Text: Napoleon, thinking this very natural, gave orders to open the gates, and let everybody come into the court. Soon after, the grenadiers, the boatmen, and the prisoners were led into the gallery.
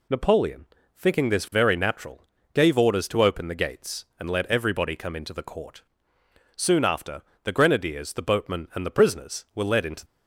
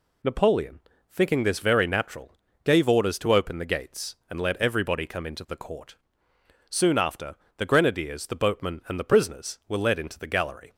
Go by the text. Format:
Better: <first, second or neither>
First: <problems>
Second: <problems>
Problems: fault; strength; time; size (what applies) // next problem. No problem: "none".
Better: second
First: stops before "the gallery"; at 10.0 s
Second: none